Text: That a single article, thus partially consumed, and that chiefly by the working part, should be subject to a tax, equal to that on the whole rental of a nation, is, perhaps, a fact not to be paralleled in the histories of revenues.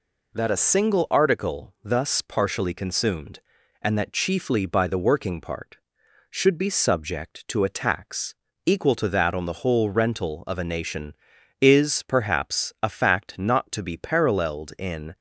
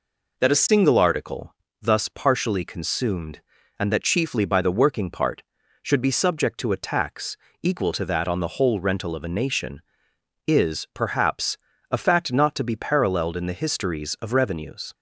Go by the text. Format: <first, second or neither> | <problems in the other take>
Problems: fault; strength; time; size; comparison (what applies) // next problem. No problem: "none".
second | stops before "the histories of revenues"; at 15.1 s